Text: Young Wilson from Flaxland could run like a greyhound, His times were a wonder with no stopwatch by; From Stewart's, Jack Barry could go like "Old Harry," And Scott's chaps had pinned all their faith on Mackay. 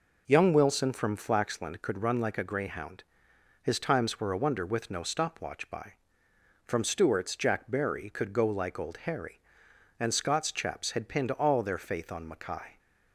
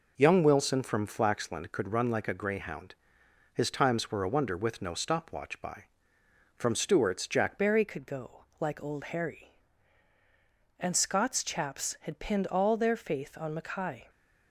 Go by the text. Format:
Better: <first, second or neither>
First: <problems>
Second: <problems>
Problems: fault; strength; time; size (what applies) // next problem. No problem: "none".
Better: first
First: none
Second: changes voice at "Barry"; from 7.5 s on; 6.5 s long // pauses between "go" and "like"; slight; at 8.4 s; 0.16 s long